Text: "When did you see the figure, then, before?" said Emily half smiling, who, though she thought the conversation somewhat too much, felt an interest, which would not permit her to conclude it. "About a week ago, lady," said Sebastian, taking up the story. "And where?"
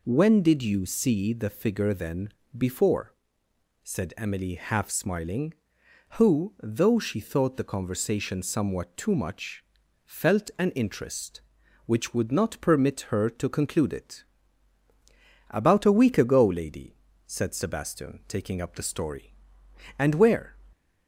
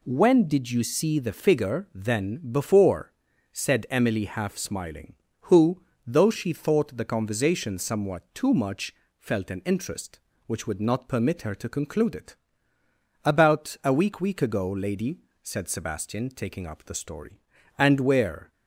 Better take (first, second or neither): first